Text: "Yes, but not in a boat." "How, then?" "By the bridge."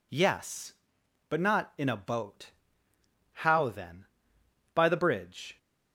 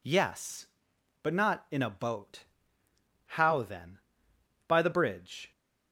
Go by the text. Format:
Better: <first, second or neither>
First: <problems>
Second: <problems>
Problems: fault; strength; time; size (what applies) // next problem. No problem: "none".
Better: neither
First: none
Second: none